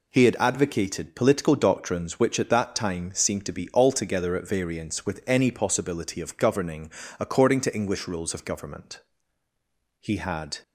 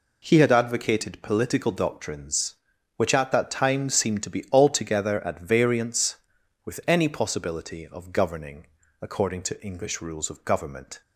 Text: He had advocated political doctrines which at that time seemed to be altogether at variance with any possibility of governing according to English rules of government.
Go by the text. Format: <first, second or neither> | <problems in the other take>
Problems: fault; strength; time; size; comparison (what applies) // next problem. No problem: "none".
second | pauses between "governing" and "according"; slight; at 6.9 s; 0.30 s long; slight in the second // goes on to say "He had"; from 10.0 s on; 0.58 s long